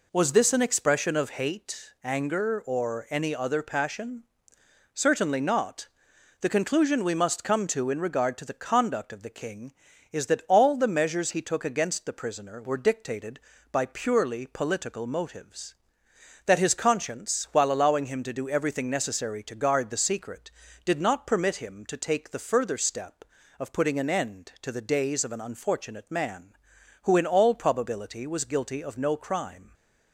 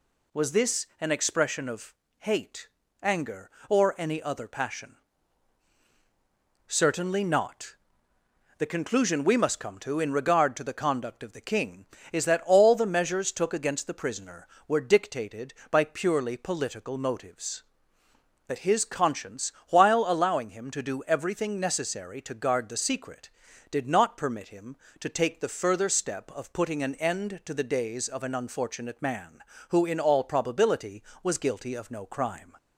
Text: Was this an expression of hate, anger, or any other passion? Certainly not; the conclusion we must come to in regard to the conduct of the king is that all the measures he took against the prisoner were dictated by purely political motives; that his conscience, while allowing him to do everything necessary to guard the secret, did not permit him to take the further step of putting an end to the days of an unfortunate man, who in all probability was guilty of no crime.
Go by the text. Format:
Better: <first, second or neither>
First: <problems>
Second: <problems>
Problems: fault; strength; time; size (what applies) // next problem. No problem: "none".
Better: first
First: none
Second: pauses between "of" and "hate"; slight; at 1.9 s; 0.26 s long // skips "he"; at 13.3 s